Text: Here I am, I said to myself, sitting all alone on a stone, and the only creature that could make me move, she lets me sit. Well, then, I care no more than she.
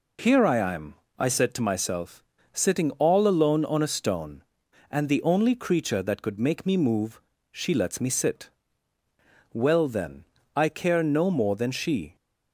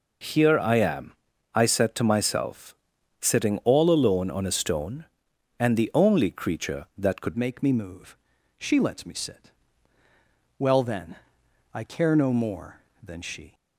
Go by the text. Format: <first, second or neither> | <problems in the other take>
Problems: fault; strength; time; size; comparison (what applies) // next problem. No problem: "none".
first | changes voice at "make"; from 7.3 s on; 6.2 s long